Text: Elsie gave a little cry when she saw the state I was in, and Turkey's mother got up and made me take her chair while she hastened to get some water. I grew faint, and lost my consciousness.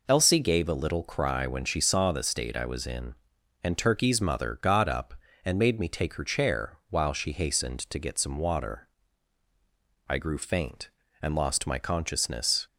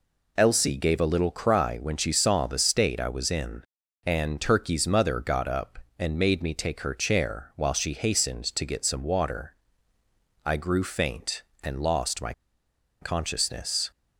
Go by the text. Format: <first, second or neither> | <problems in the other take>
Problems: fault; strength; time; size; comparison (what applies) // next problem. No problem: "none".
first | pauses between "my" and "consciousness"; noticeable; at 12.3 s; 0.67 s long